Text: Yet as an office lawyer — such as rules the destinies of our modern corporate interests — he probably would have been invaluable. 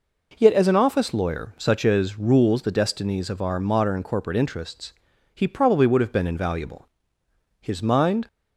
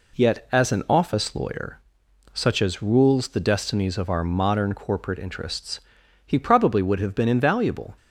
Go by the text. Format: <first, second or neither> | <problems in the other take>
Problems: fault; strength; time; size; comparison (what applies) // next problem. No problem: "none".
second | goes on to say "His mind"; noticeable; from 7.6 s on; 0.66 s long